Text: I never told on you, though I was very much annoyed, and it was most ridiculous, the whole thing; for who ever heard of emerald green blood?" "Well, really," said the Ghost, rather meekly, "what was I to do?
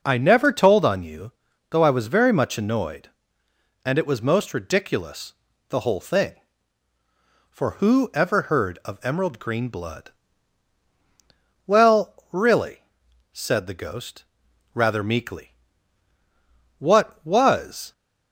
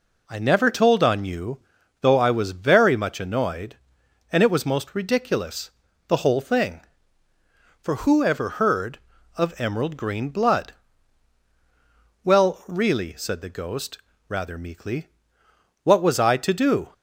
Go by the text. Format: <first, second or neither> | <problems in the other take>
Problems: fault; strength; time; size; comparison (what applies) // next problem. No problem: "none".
second | stops before "I to do"; at 17.9 s